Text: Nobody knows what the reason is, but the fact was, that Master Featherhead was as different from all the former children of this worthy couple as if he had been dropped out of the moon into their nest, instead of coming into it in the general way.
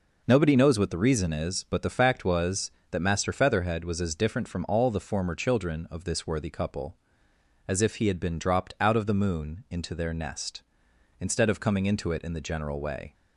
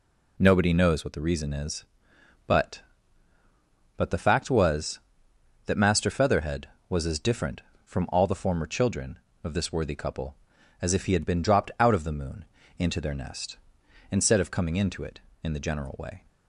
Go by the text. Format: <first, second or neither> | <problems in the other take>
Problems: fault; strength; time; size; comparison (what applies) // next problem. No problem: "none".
first | says "but" twice; at 3.9 s // pauses between "moon" and "into"; slight; at 12.4 s; 0.34 s long